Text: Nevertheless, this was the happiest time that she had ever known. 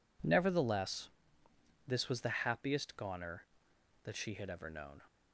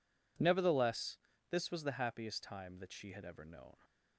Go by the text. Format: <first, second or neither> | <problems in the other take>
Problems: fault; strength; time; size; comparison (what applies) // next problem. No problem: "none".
second | says "goner" for "time"; at 2.9 s